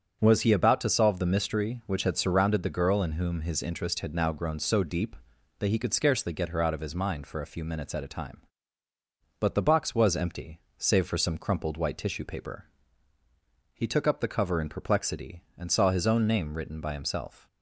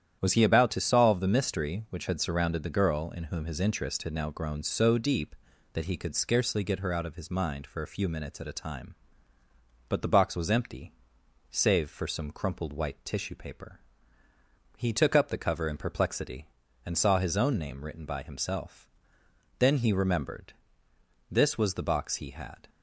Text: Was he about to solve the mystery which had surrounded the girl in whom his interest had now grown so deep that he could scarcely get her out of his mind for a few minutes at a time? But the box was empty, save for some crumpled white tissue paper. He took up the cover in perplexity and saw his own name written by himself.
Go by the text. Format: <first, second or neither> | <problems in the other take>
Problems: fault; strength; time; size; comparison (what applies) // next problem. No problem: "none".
first | starts louder than the rest; strong; until 1.2 s; 10 dB; strong in the first // goes on to say "Then he remembered This was the box he had"; strong; from 19.5 s on; 3.1 s long